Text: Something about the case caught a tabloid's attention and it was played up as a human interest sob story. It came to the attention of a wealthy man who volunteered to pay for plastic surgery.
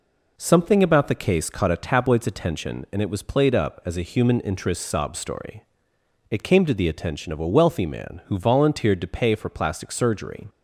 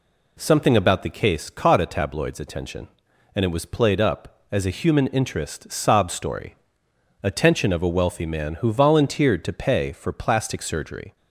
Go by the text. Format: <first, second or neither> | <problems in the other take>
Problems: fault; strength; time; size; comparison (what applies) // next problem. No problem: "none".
first | skips "It came to the"; at 6.8 s